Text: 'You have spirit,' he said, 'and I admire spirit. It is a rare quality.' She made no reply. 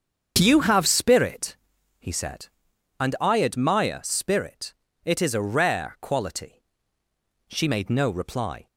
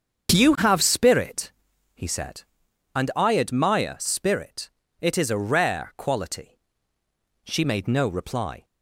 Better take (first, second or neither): neither